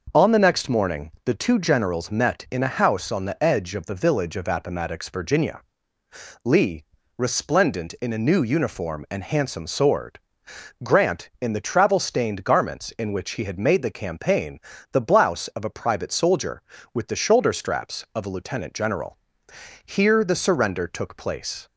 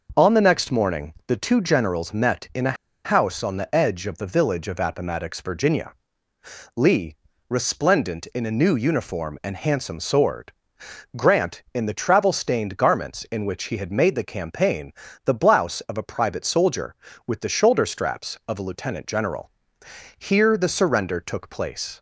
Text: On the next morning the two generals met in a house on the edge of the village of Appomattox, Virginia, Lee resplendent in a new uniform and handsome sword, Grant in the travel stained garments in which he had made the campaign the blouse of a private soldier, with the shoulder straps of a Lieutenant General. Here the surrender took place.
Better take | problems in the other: first | pauses between "a" and "house"; slight; at 2.7 s; 0.30 s long // pauses between "Lee" and "resplendent"; slight; at 7.1 s; 0.32 s long; slight in the first // pauses between "campaign" and "the"; slight; at 14.9 s; 0.32 s long; slight in the first

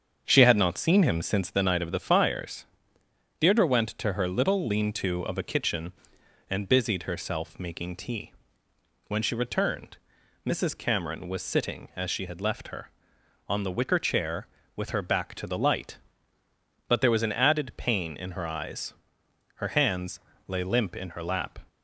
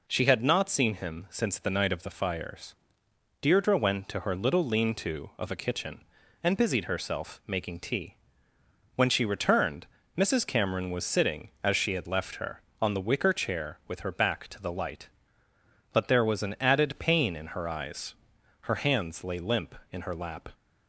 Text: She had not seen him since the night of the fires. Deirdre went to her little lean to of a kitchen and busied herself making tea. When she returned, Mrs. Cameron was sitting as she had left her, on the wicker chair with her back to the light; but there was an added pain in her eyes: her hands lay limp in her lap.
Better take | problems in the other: second | starts louder than the rest; strong; until 1.6 s; 7.5 dB // pauses between "hands" and "lay"; slight; at 20.1 s; 0.30 s long

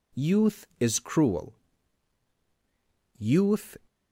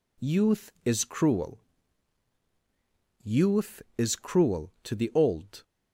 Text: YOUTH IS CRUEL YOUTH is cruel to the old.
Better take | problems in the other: second | pauses between "CRUEL" and "YOUTH"; strong; at 1.5 s; 1.6 s long; strong in the second // stops before "is cruel to the old"; at 3.8 s

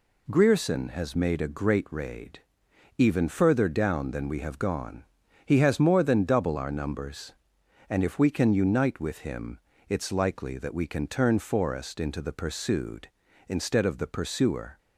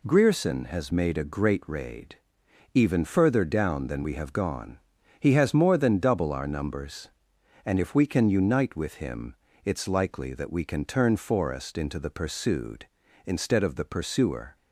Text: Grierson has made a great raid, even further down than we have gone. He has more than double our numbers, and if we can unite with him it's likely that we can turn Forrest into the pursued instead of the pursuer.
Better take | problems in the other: neither | pauses between "him" and "it's"; slight; the same in both

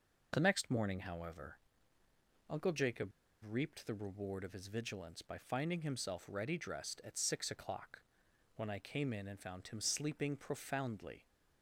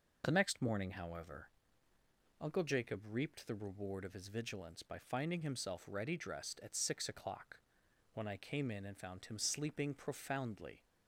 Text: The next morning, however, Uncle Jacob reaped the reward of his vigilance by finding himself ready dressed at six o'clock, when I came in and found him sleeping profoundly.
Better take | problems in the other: second | pauses between "Jacob" and "reaped"; at 3.0 s; 0.36 s long

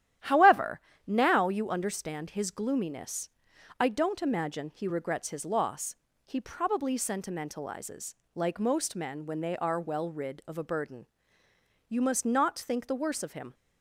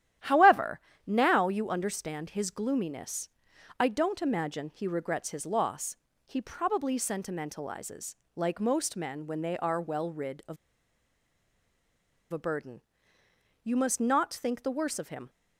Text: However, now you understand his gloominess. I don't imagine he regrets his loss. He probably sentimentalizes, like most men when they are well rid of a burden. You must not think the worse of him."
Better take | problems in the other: first | starts louder than the rest; strong; until 1.4 s; 11.5 dB; strong in the first // pauses between "of" and "a"; strong; at 10.5 s; 1.7 s long

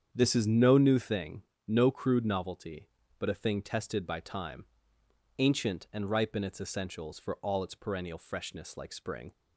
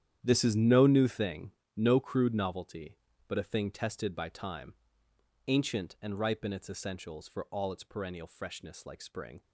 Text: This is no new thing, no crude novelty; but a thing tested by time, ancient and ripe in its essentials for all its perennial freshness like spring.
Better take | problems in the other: first | gets quieter; strong; throughout; 14 dB // starts louder than the rest; strong; until 1.2 s; 10 dB; strong in the first

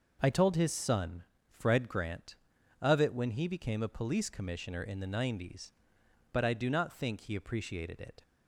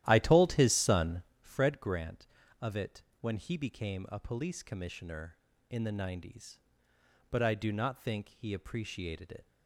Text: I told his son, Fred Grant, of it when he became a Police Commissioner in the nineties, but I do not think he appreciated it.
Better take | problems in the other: first | starts louder than the rest; strong; until 1.5 s; 13 dB // pauses between "it" and "when"; slight; at 3.0 s; 0.20 s long

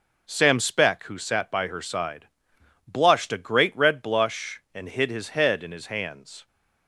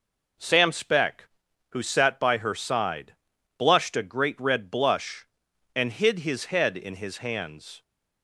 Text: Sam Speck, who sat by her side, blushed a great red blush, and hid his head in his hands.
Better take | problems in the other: neither | none

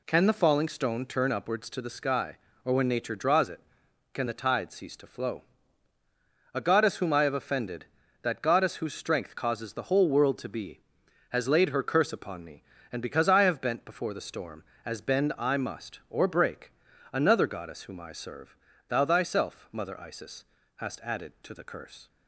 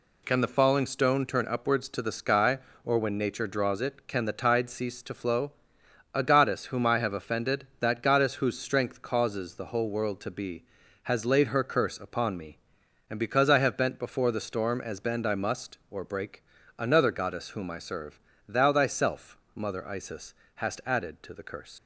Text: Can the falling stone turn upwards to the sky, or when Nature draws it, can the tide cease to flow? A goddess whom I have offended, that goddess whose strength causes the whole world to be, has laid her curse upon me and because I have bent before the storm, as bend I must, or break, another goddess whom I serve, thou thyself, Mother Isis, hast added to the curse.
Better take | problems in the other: first | leaves "curse" unfinished; at 21.7 s; 110 ms

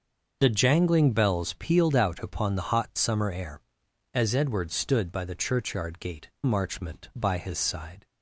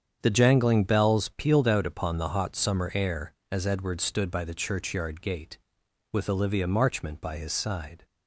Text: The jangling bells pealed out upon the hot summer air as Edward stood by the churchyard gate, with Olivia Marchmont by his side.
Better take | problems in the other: second | starts louder than the rest; until 1.4 s; 6.5 dB; strong in the second // skips "with Olivia"; at 6.3 s

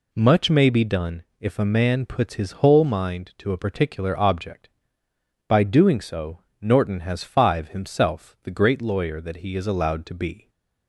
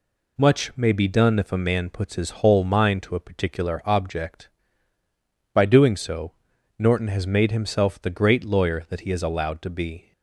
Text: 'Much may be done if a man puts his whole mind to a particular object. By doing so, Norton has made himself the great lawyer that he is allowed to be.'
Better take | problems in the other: second | pauses between "done" and "if"; slight; at 1.2 s; 0.16 s long // says "five" for "made"; at 7.2 s

